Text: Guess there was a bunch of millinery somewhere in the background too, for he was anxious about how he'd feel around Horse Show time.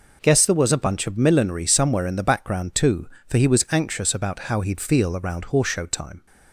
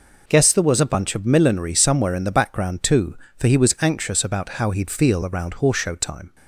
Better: neither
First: none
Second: none

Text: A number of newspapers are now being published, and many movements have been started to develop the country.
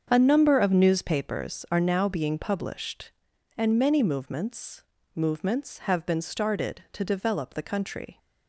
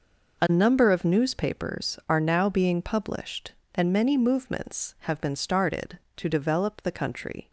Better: second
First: starts louder than the rest; strong; until 1.1 s; 7 dB // says "movements" twice; at 5.1 s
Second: none

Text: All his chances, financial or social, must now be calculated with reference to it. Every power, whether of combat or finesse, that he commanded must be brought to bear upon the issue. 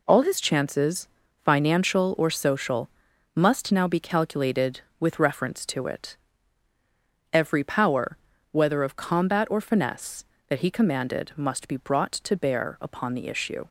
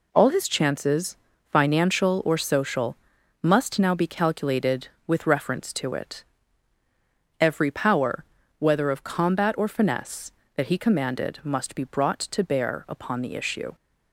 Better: neither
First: none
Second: none

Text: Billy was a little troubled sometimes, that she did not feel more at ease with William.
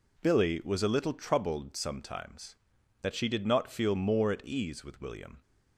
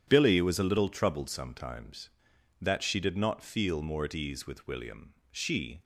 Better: first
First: none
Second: starts louder than the rest; strong; until 1.0 s; 9.5 dB // goes on to say "She"; from 5.3 s on; 0.52 s long

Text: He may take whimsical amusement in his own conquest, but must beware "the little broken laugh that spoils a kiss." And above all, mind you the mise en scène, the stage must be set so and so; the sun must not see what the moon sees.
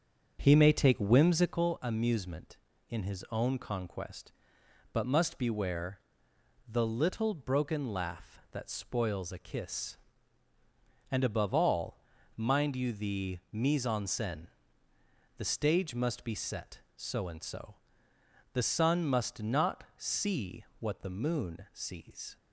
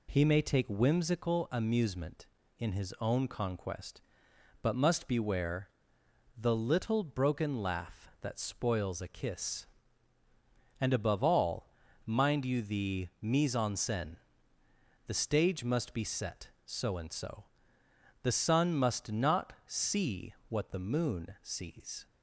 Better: second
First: starts louder than the rest; until 1.8 s; 7 dB // pauses between "beware" and "the"; noticeable; at 6.0 s; 0.66 s long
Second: pauses between "beware" and "the"; noticeable; at 5.6 s; 0.66 s long

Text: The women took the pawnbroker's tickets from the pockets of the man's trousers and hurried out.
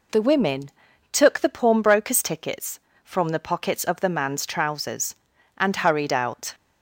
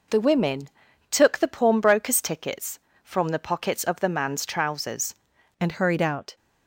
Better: first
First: pauses between "women" and "took"; at 0.6 s; 0.42 s long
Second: pauses between "women" and "took"; at 0.6 s; 0.42 s long // changes voice at "and"; from 5.5 s on; 0.8 s long

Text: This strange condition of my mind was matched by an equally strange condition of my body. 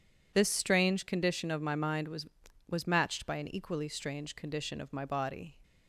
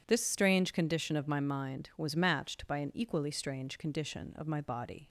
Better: second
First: says "was" twice; at 2.7 s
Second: none

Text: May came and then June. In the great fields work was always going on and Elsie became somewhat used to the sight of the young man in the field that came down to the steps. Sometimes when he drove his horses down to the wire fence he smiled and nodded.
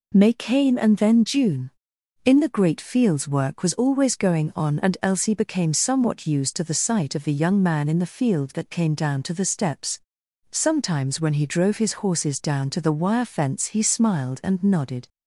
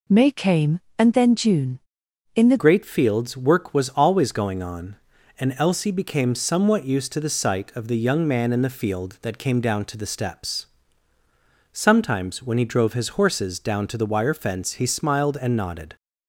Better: first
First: none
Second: changes voice at "great"; from 2.5 s on; 13.4 s long

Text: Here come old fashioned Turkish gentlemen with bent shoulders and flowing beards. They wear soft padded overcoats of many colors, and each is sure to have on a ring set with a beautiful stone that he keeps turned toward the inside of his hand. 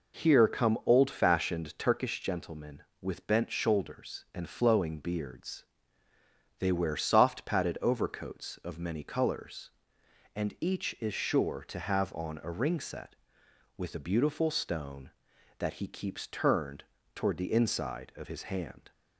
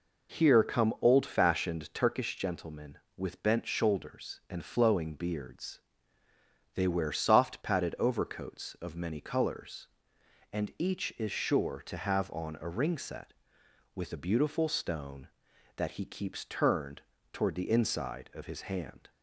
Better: neither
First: pauses between "turned" and "toward"; slight; at 16.8 s; 0.32 s long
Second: pauses between "turned" and "toward"; slight; at 17.0 s; 0.32 s long

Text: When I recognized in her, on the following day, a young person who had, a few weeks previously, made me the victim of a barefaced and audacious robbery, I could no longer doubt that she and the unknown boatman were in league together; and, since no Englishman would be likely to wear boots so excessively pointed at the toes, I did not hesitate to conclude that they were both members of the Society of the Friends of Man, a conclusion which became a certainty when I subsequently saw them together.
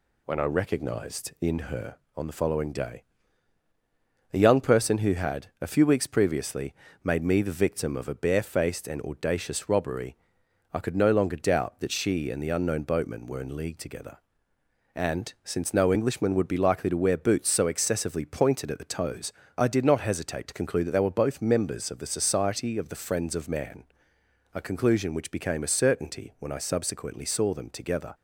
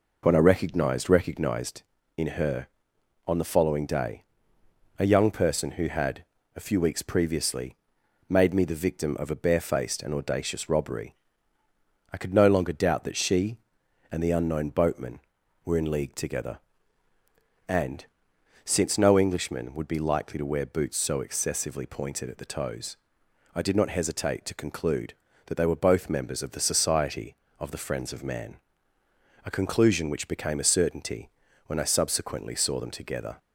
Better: first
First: none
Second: says "recognized" twice; at 1.1 s // pauses between "certainty" and "when"; at 31.2 s; 0.38 s long

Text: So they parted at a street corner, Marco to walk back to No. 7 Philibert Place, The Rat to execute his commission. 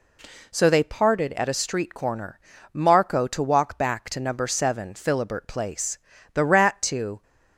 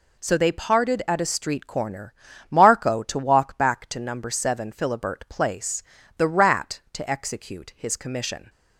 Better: second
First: stops before "execute his commission"; at 7.2 s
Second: none

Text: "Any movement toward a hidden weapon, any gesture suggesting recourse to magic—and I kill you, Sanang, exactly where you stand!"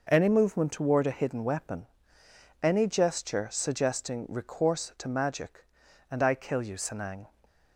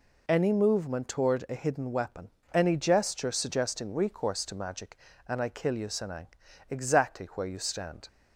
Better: second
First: stops before "exactly where you stand"; at 7.4 s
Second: none

